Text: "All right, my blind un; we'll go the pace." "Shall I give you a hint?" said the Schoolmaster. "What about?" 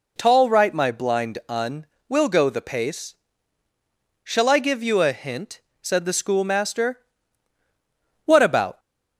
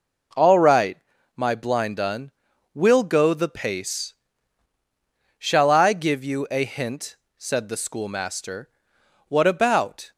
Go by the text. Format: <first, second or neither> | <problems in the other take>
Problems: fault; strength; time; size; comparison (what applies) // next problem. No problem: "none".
second | says "Tall" for "All"; at 0.1 s